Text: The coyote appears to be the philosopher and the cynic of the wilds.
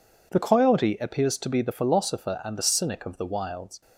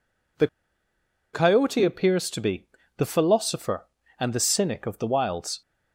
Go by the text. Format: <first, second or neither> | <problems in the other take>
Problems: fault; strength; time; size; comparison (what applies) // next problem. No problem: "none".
first | pauses between "The" and "coyote"; noticeable; at 0.4 s; 0.86 s long // pauses between "be" and "the"; slight; at 2.6 s; 0.26 s long